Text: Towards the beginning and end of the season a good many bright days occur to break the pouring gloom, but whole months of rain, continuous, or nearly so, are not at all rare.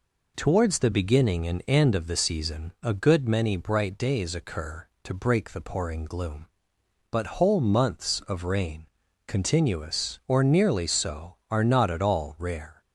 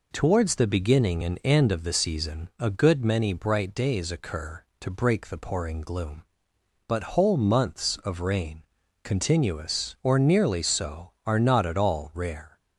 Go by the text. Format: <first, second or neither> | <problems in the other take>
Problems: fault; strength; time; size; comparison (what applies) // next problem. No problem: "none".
neither | none